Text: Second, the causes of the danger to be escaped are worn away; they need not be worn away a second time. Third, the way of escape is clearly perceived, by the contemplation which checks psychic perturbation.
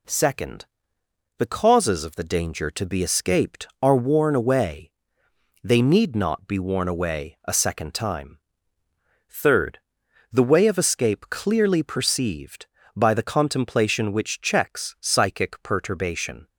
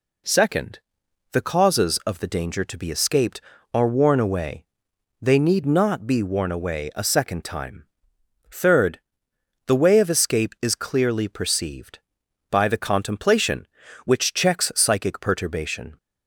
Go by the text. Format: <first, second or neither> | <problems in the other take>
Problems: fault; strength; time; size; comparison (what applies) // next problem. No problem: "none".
second | skips "is"; at 11.2 s